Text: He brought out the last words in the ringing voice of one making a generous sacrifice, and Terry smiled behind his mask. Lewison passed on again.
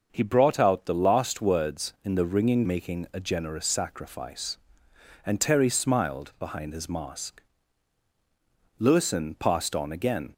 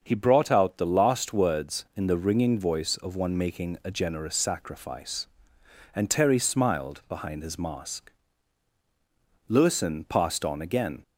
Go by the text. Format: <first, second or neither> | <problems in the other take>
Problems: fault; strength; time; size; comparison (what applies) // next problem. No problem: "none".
second | starts louder than the rest; until 1.1 s; 6 dB; also in the second // skips "voice of one"; at 2.6 s